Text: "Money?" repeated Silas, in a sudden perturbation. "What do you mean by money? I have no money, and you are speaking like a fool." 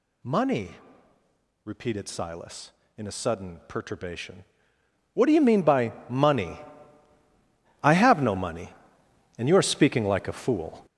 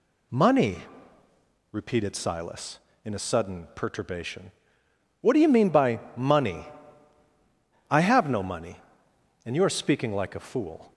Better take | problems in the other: second | gets louder; strong; throughout; 8 dB // pauses between "by" and "money"; slight; at 5.9 s; 0.16 s long; slight in the second

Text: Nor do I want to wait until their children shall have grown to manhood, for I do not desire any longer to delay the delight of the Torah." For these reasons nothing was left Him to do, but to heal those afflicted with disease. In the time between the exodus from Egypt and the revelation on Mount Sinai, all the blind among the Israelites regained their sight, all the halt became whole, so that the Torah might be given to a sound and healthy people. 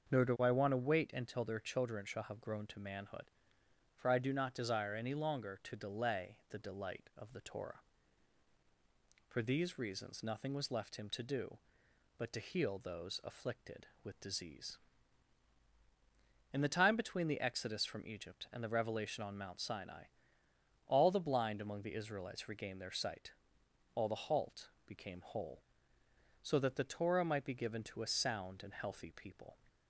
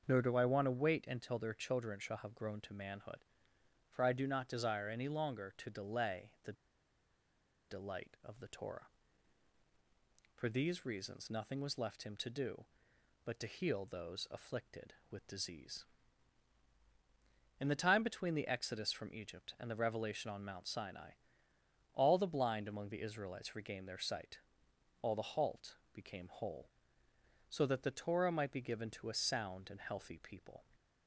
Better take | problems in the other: first | starts louder than the rest; until 1.0 s; 6.5 dB; also in the first // pauses between "the" and "delight"; at 6.5 s; 1.1 s long // pauses between "halt" and "became"; slight; at 25.7 s; 0.16 s long; slight in the first

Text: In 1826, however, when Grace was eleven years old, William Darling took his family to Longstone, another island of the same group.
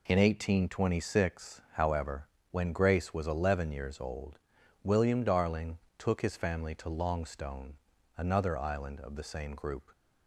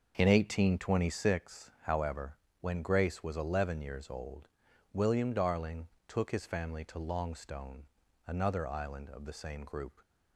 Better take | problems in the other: first | starts louder than the rest; noticeable; until 1.4 s; 6 dB // pauses between "Darling" and "took"; slight; at 5.8 s; 0.20 s long; slight in the first

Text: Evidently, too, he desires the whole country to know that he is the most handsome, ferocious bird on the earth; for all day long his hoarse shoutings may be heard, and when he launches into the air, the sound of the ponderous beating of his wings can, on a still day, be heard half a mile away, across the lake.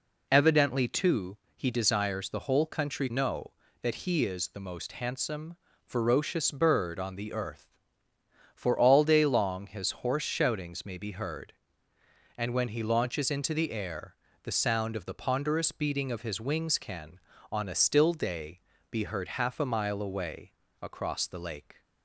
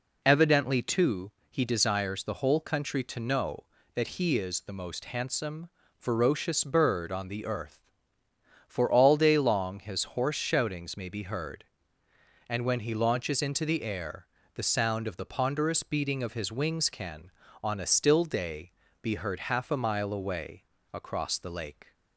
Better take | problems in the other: second | skips "to"; at 3.0 s

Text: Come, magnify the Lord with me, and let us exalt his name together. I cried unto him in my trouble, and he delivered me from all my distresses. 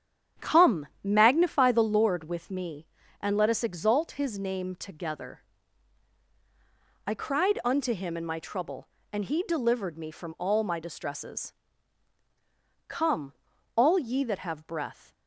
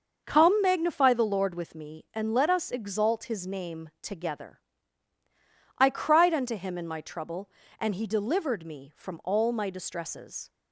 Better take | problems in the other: second | starts louder than the rest; strong; until 1.5 s; 9 dB; also in the second // goes on to say "Come all ye that have breath"; strong; from 12.8 s on; 2.2 s long

